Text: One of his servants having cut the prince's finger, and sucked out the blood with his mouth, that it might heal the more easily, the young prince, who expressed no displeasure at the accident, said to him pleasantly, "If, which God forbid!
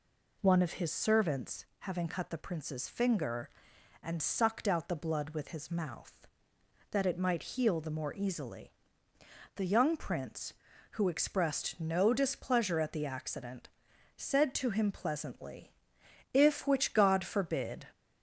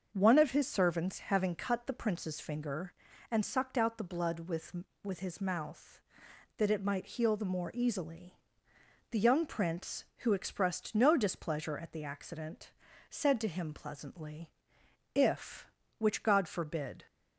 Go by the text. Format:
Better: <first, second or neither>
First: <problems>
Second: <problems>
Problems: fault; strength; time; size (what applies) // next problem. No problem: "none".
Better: first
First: none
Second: starts louder than the rest; until 1.1 s; 6.5 dB // says "with" twice; at 5.0 s